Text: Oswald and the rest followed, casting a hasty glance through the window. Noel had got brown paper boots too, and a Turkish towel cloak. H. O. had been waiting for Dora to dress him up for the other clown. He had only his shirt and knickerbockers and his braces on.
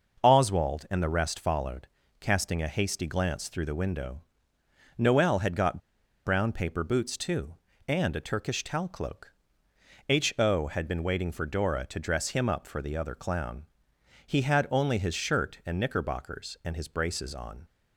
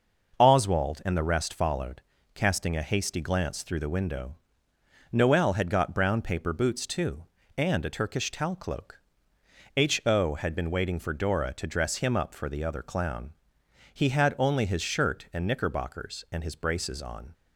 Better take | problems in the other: second | starts louder than the rest; noticeable; until 1.2 s; 6 dB; noticeable in the second // pauses between "got" and "brown"; noticeable; at 5.7 s; 0.47 s long

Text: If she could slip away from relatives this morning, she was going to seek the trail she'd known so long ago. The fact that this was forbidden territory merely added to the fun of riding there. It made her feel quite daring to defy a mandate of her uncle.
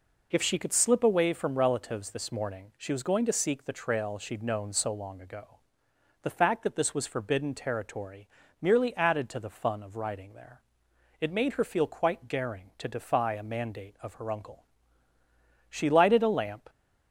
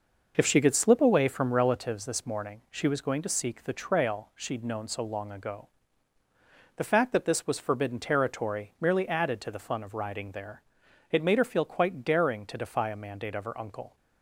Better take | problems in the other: second | pauses between "territory" and "merely"; slight; at 8.2 s; 0.32 s long // goes on to say "She lighted a lamp"; noticeable; from 15.6 s on; 1.0 s long

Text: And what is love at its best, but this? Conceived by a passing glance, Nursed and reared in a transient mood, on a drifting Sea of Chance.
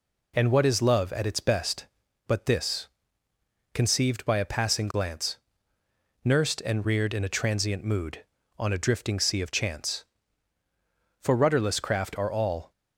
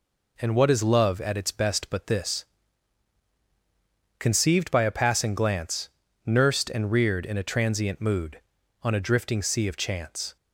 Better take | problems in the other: second | goes on to say "For rudderless craft are all"; from 11.1 s on; 1.5 s long

